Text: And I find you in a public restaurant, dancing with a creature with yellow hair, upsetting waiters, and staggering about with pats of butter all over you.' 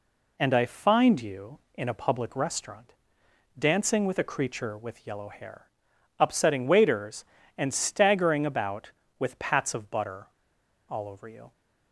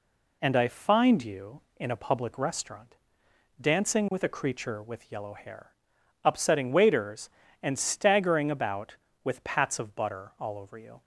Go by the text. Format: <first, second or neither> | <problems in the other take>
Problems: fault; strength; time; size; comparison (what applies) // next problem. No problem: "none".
second | pauses between "butter" and "all"; noticeable; at 10.2 s; 0.63 s long